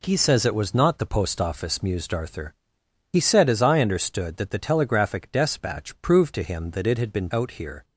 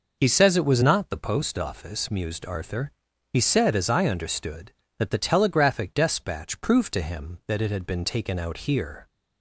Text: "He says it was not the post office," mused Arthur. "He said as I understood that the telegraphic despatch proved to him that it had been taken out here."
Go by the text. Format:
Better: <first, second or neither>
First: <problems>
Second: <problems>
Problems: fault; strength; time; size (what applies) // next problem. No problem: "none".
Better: second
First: skips "taken"; at 7.3 s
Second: none